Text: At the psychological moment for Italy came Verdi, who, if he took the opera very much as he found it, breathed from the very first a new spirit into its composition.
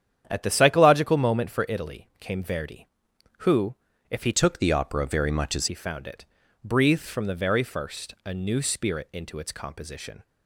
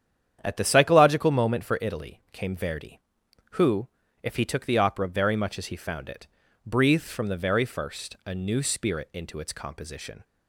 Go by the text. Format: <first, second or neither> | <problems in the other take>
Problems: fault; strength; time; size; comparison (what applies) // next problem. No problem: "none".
second | starts louder than the rest; strong; until 1.2 s; 9 dB; strong in the second // changes voice from "took" to "as"; from 4.3 to 5.6 s; 1.3 s long